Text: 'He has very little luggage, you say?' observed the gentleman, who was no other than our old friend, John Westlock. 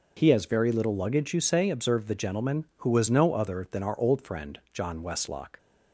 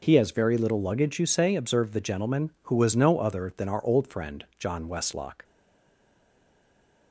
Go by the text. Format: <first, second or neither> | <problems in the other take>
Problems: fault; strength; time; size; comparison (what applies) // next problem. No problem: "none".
first | stays silent after the last word; noticeable; from 5.4 s on; 1.7 s long